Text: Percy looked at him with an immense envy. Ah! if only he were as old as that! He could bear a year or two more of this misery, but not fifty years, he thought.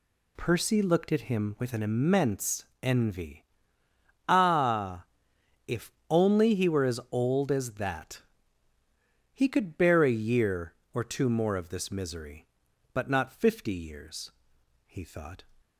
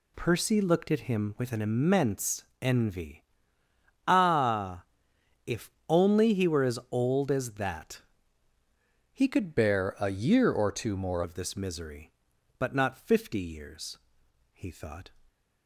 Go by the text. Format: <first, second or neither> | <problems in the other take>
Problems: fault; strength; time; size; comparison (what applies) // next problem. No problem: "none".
first | pauses between "immense" and "envy"; slight; at 2.4 s; 0.18 s long; slight in the first // pauses between "if" and "only"; slight; at 5.6 s; 0.18 s long; slight in the first // changes voice from "bear" to "more"; from 9.5 to 11.2 s; 1.7 s long